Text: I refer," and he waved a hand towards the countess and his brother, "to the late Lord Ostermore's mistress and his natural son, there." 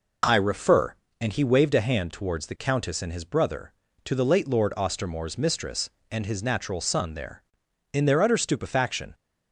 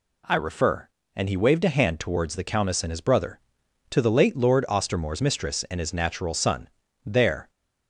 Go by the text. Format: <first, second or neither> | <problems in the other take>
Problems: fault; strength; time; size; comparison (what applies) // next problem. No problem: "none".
second | goes on to say "In their utter stupefaction"; noticeable; from 7.9 s on; 1.2 s long